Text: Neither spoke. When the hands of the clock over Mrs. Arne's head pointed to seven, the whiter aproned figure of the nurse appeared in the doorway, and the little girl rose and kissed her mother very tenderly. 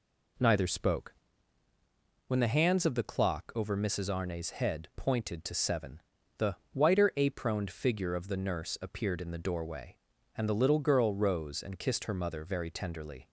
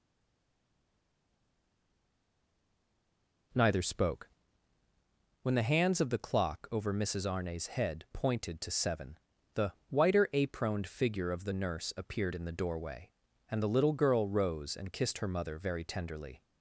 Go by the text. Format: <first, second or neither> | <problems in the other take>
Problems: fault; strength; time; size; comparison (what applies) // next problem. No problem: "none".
first | stays silent before the first word; strong; until 3.5 s; 3.5 s long // pauses between "the" and "whiter"; slight; at 9.7 s; 0.16 s long; slight in the first